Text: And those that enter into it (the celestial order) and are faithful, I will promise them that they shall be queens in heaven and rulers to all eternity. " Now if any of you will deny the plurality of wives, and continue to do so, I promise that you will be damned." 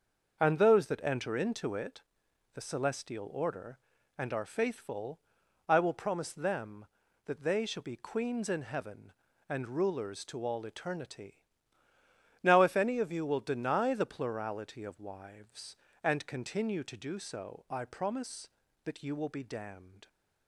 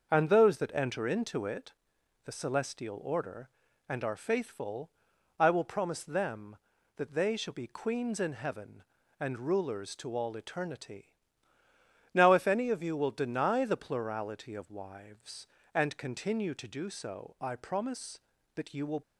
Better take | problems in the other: first | starts louder than the rest; until 1.1 s; 6.5 dB; also in the first // stops before "be damned"; at 19.0 s

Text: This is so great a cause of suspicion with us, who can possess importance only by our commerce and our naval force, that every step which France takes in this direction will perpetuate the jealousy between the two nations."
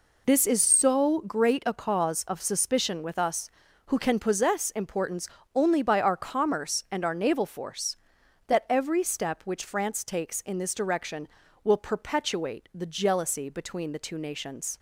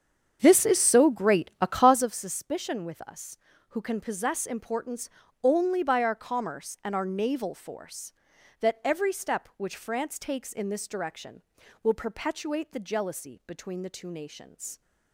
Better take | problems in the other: first | starts louder than the rest; strong; until 2.2 s; 8 dB // pauses between "importance" and "only"; slight; at 5.1 s; 0.32 s long; slight in the first

